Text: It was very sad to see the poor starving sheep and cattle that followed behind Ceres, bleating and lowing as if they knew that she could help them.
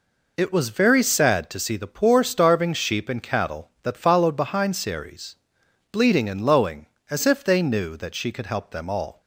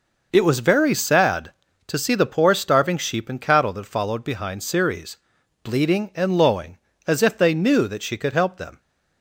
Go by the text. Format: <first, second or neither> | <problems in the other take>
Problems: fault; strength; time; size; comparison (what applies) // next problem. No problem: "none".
second | goes on to say "All"; slight; from 8.8 s on; 0.32 s long